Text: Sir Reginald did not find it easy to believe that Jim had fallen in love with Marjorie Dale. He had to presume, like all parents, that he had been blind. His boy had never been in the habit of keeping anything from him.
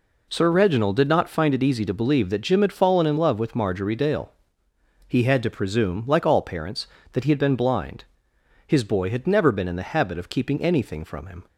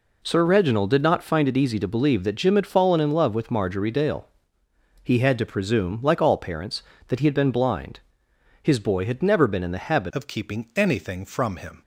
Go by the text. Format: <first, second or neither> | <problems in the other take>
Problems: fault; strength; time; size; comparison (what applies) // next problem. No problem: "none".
first | changes voice at "of"; from 10.1 s on; 1.7 s long